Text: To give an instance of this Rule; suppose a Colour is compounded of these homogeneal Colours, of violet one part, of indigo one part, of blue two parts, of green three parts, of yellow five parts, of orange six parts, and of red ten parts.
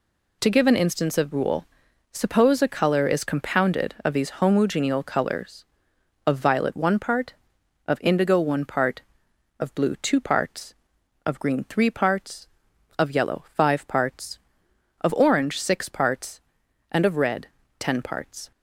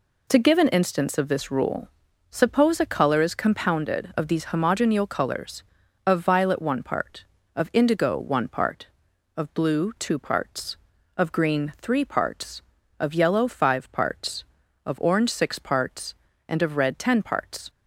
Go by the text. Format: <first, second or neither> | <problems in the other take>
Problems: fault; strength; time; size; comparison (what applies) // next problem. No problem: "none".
second | skips "this"; at 1.3 s // pauses between "red" and "ten"; slight; at 17.4 s; 0.32 s long